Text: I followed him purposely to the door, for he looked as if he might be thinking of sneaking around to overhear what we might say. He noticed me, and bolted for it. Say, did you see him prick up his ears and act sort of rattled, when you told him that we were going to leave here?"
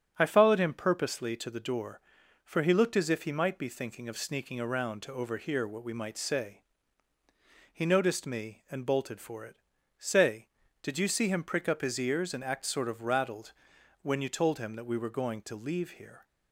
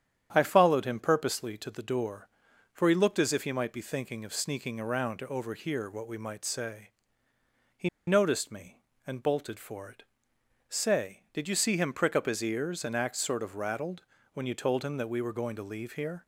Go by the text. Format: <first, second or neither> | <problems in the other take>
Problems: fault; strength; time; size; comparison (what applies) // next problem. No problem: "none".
first | starts louder than the rest; strong; until 1.3 s; 9.5 dB; strong in the first // pauses between "He" and "noticed"; slight; at 7.8 s; 0.18 s long